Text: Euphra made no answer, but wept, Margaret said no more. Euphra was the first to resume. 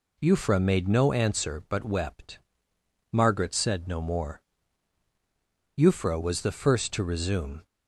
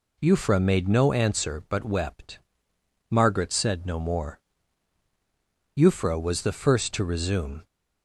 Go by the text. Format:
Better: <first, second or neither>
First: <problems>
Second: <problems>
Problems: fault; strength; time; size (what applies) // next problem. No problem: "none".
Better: neither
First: none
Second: none